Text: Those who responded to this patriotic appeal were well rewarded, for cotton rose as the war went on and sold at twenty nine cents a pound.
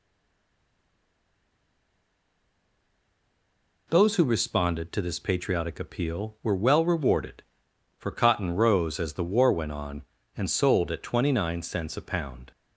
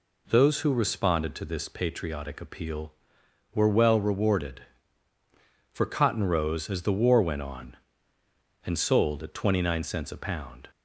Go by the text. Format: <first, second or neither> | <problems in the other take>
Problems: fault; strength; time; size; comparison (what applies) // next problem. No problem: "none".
second | stays silent before the first word; strong; until 3.8 s; 3.8 s long